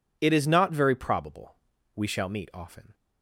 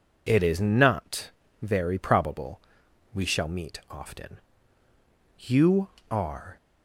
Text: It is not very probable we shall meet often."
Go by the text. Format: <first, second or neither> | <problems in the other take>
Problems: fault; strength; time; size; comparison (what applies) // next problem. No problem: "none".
first | pauses between "not" and "very"; slight; at 1.2 s; 0.32 s long // pauses between "probable" and "we"; noticeable; at 2.5 s; 0.56 s long; also in the first // goes on to say "You are"; noticeable; from 5.3 s on; 1.1 s long